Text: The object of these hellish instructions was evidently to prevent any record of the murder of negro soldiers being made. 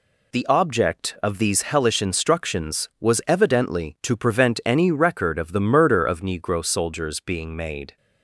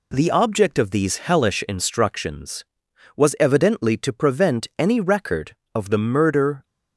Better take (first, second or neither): first